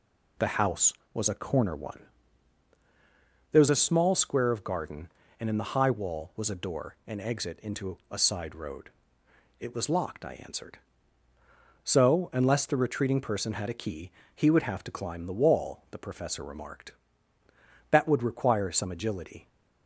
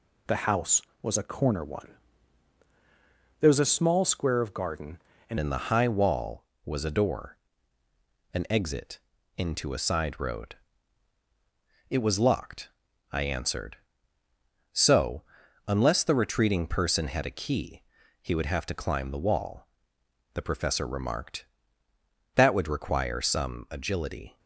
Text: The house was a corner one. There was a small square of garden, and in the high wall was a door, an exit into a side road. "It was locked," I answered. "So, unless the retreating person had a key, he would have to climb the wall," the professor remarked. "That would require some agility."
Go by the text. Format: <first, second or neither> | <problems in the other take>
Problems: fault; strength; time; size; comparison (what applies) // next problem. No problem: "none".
first | changes voice at "in"; from 5.4 s on; 18.9 s long // pauses between "exit" and "into"; slight; at 9.0 s; 0.36 s long